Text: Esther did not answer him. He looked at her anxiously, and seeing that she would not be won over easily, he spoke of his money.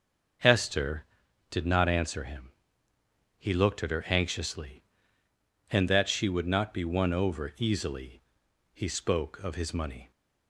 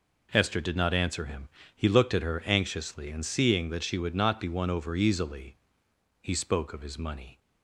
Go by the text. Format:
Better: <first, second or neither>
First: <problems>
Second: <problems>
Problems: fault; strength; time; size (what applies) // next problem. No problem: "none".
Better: second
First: starts louder than the rest; noticeable; until 1.8 s; 6 dB // skips "seeing"; at 5.8 s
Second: none